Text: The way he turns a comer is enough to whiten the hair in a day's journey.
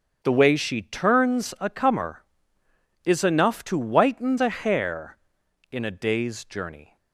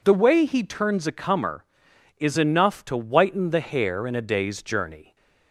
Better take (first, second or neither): second